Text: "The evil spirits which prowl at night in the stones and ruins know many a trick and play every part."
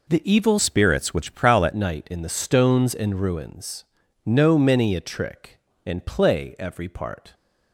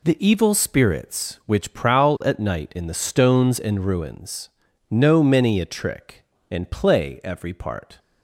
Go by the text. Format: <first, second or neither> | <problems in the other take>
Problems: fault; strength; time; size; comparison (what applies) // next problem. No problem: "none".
second | changes voice from "spirits" to "at"; from 0.5 to 1.7 s; 1.2 s long // pauses between "ruins" and "know"; at 3.8 s; 0.40 s long; also in the second